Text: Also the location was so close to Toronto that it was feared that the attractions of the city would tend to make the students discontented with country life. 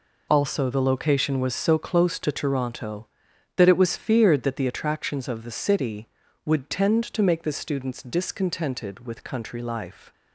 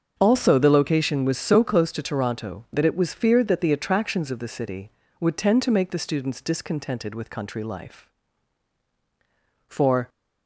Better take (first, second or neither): first